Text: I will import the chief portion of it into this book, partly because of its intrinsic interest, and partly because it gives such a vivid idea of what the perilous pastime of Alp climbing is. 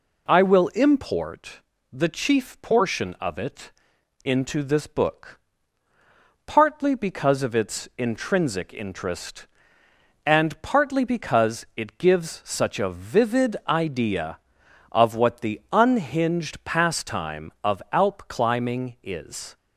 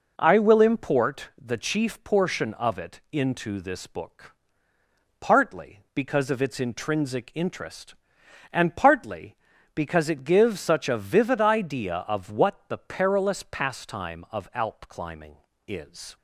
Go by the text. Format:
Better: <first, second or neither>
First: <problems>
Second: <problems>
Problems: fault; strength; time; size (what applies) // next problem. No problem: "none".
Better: second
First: pauses between "import" and "the"; slight; at 1.6 s; 0.32 s long // pauses between "it" and "into"; noticeable; at 3.7 s; 0.54 s long // says "unhinged" for "perilous"; at 15.7 s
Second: none